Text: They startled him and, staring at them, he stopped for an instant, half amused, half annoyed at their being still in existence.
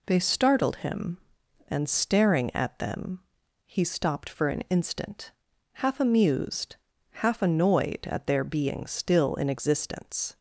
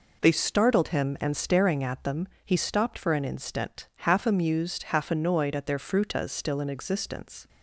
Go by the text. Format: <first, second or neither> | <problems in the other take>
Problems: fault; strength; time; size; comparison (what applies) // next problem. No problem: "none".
first | says "frutas" for "being"; at 5.7 s